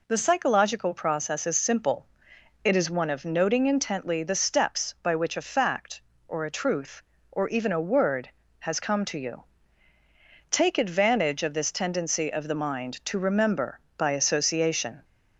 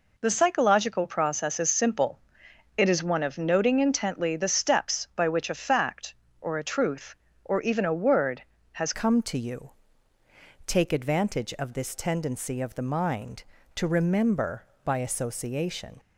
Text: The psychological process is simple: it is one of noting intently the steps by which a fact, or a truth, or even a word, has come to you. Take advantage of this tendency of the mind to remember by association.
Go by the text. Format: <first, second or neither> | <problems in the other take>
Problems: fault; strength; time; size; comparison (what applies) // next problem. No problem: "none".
first | changes voice at "come"; from 8.9 s on; 7.0 s long